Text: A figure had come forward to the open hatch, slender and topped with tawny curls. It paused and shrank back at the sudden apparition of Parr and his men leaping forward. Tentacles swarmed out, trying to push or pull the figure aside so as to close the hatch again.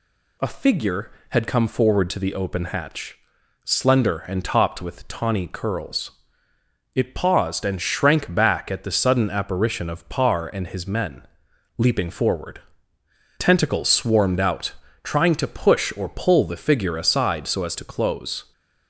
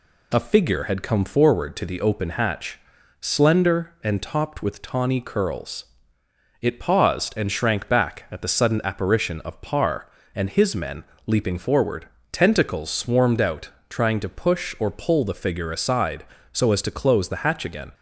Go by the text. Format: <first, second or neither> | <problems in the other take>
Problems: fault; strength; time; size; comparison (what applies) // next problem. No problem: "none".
second | pauses between "men" and "leaping"; noticeable; at 11.2 s; 0.50 s long; slight in the second // stops before "the hatch again"; at 18.5 s